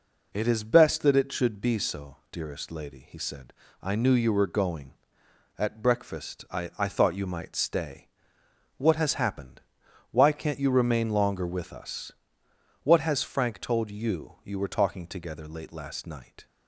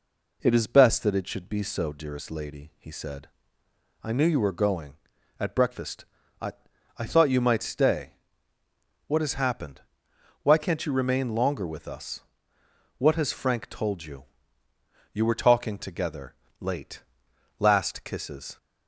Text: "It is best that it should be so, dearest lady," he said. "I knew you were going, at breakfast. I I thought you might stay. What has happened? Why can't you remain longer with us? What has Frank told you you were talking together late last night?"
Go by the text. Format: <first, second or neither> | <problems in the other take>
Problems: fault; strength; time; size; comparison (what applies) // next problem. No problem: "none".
first | pauses between "I" and "I"; noticeable; at 6.5 s; 0.46 s long // pauses between "you" and "you"; noticeable; at 14.2 s; 0.88 s long // pauses between "together" and "late"; slight; at 16.3 s; 0.24 s long // pauses between "late" and "last"; noticeable; at 17.0 s; 0.56 s long // says "kisses" for "night"; at 18.0 s